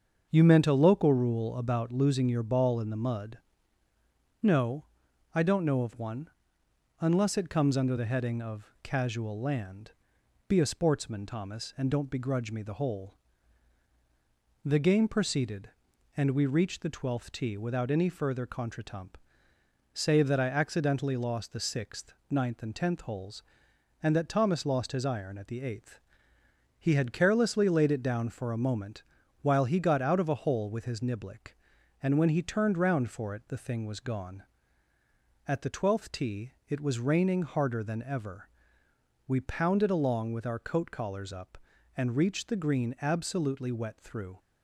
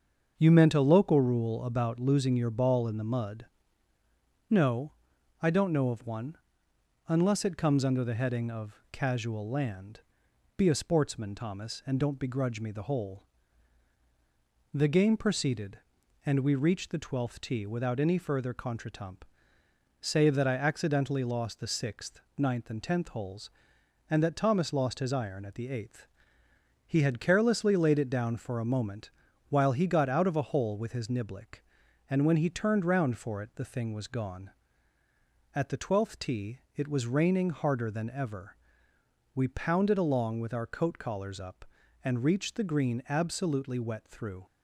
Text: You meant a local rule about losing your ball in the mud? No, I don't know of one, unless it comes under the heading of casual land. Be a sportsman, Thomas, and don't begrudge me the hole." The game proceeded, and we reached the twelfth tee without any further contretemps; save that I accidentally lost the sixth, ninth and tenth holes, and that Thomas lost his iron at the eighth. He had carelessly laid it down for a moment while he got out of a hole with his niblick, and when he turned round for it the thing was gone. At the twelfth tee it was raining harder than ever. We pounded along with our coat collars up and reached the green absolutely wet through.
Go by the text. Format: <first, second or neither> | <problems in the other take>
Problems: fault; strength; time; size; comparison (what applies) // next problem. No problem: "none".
neither | starts louder than the rest; the same in both // pauses between "moment" and "while"; the same in both // pauses between "tee" and "it"; slight; the same in both